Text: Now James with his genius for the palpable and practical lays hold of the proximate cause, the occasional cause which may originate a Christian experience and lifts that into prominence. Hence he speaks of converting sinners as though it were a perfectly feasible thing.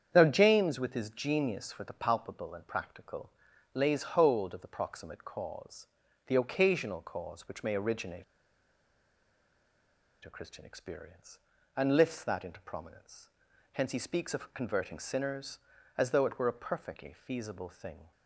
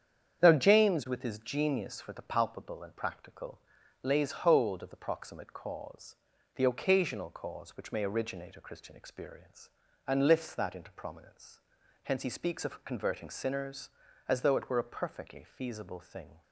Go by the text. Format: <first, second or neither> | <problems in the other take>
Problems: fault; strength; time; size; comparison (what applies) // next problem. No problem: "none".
second | starts louder than the rest; strong; until 1.1 s; 8 dB; strong in the second // pauses between "practical" and "lays"; at 3.3 s; 0.42 s long; also in the second // pauses between "originate" and "a"; strong; at 8.2 s; 2.0 s long